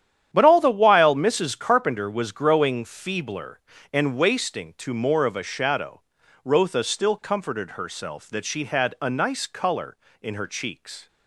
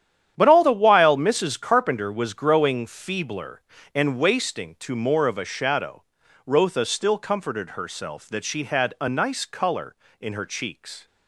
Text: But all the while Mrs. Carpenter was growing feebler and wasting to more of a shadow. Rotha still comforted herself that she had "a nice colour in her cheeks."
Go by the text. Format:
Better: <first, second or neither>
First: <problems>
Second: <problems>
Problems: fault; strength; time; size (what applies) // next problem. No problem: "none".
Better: neither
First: starts louder than the rest; strong; until 1.3 s; 9.5 dB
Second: starts louder than the rest; strong; until 1.3 s; 9.5 dB